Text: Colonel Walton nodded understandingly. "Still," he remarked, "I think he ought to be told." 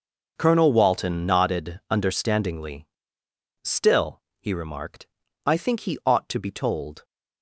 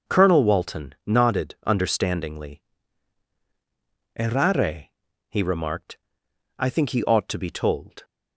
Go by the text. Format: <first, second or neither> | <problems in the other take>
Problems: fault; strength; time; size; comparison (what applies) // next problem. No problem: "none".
first | starts louder than the rest; noticeable; until 1.2 s; 6 dB // says "Errare" for "Still"; at 4.1 s